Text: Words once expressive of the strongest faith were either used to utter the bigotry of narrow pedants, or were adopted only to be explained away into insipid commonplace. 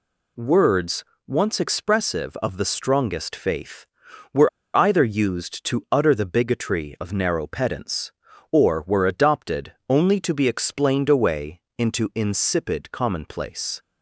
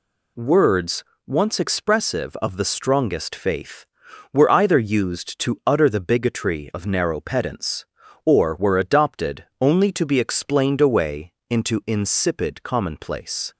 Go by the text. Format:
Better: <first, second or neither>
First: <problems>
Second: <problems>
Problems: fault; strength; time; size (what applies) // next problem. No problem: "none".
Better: second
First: pauses between "Words" and "once"; slight; at 1.0 s; 0.24 s long // pauses between "were" and "either"; slight; at 4.4 s; 0.26 s long // pauses between "adopted" and "only"; slight; at 9.7 s; 0.16 s long // pauses between "away" and "into"; slight; at 11.6 s; 0.16 s long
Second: pauses between "Words" and "once"; slight; at 1.0 s; 0.24 s long // pauses between "adopted" and "only"; slight; at 9.4 s; 0.16 s long // pauses between "away" and "into"; slight; at 11.3 s; 0.16 s long